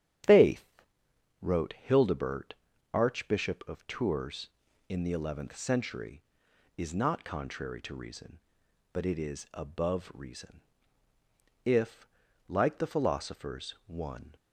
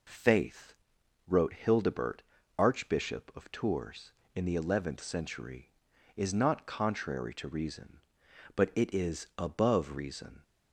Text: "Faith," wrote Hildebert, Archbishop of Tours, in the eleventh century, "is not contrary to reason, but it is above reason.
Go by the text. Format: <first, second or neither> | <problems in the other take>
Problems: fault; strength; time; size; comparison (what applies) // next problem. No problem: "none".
second | starts louder than the rest; strong; until 1.9 s; 10 dB // goes on to say "If like the philosophers one"; strong; from 11.6 s on; 2.7 s long